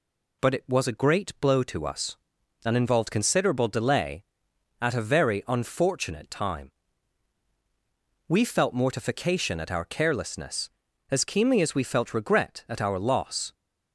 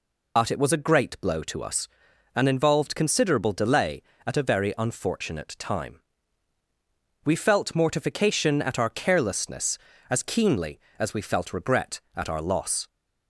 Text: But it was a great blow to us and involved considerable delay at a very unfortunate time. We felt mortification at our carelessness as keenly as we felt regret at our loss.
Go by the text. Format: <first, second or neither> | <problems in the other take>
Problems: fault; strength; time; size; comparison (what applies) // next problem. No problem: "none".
first | loses the start of "But"; at 0.3 s; 85 ms